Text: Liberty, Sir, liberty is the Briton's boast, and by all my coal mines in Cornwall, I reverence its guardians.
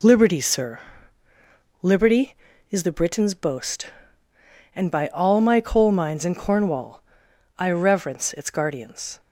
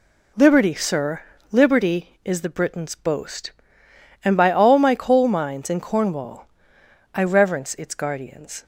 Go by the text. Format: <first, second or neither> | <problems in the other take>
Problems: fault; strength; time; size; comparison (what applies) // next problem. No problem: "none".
neither | none